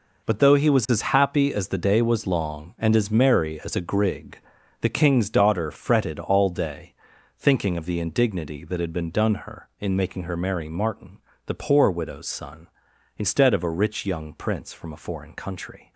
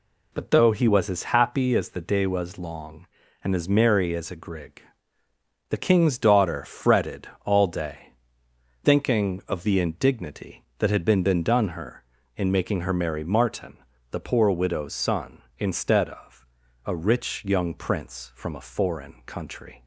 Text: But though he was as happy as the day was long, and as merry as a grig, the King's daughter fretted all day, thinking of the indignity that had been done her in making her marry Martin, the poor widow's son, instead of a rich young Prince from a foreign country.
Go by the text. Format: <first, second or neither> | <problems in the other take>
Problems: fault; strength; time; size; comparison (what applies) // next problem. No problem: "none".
first | pauses between "fretted" and "all"; slight; at 7.2 s; 0.16 s long // says "been" twice; at 11.2 s // pauses between "of" and "a"; at 16.4 s; 0.40 s long